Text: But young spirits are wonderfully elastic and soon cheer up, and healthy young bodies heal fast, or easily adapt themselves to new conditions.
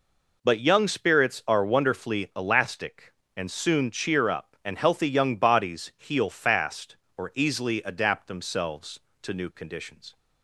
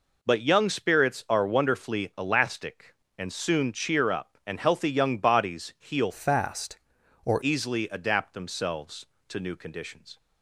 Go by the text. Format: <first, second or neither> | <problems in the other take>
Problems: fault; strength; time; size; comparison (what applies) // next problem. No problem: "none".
first | changes voice from "fast" to "or"; from 6.1 to 7.4 s; 1.3 s long